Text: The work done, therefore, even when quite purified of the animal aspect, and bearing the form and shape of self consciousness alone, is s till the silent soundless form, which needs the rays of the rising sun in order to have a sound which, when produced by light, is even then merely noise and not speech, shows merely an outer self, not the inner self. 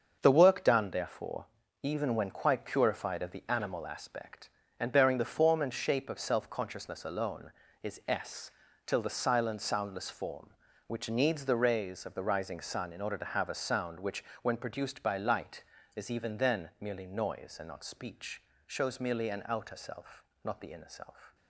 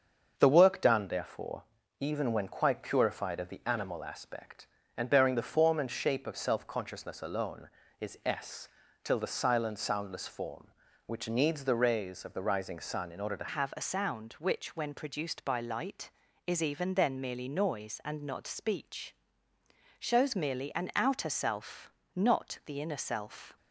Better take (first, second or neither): first